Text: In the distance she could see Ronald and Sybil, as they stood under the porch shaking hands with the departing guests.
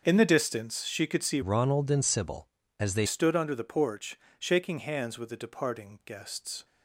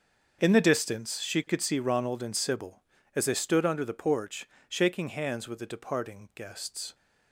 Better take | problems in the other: second | starts louder than the rest; until 1.0 s; 6.5 dB; also in the second // changes voice from "Ronald" to "they"; from 1.4 to 3.0 s; 1.6 s long // pauses between "porch" and "shaking"; slight; at 4.1 s; 0.20 s long; slight in the second

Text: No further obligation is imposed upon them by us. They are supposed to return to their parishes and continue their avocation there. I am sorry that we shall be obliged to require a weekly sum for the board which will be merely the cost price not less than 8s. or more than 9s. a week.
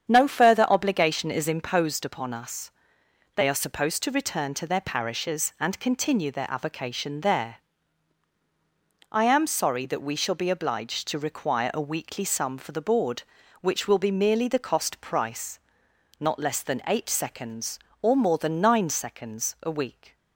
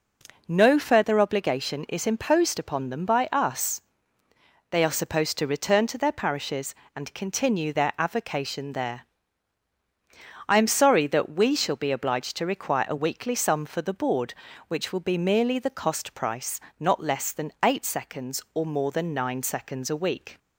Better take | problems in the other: second | starts louder than the rest; strong; until 1.1 s; 8 dB // skips "them by"; at 2.3 s // pauses between "price" and "not"; noticeable; at 15.5 s; 0.60 s long; slight in the second

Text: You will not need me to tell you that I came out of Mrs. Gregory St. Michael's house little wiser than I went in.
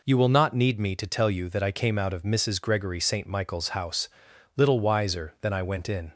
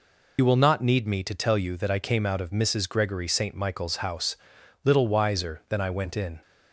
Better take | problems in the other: first | loses the start of "You"; at 0.3 s; 70 ms // pauses between "house" and "little"; noticeable; at 4.3 s; 0.48 s long; noticeable in the first

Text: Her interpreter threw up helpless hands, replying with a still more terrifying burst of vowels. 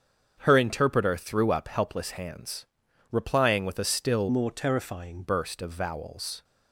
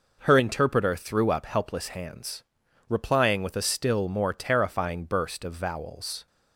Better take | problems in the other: second | starts louder than the rest; strong; until 1.4 s; 7.5 dB // changes voice from "more" to "terrifying"; from 4.3 to 5.2 s; 0.9 s long

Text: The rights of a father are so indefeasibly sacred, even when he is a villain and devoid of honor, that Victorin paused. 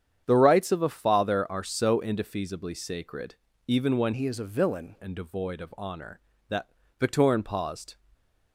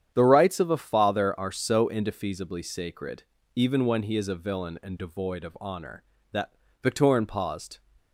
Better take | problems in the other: second | starts louder than the rest; strong; until 1.2 s; 8.5 dB; strong in the second // changes voice from "he" to "villain"; from 4.1 to 4.9 s; 0.8 s long // pauses between "that" and "Victorin"; slight; at 6.6 s; 0.32 s long; slight in the second

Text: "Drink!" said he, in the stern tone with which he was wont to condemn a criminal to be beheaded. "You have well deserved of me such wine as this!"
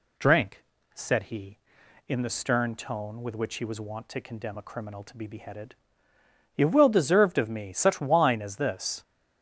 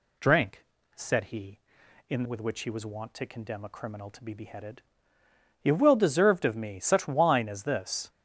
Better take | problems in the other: first | skips "the stern tone"; at 2.2 s

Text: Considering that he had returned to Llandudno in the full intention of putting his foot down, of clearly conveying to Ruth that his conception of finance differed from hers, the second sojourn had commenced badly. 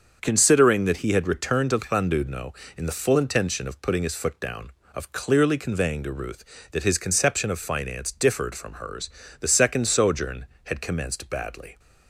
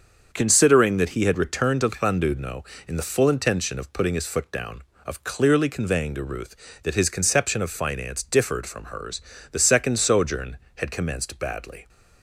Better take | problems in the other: neither | starts louder than the rest; the same in both

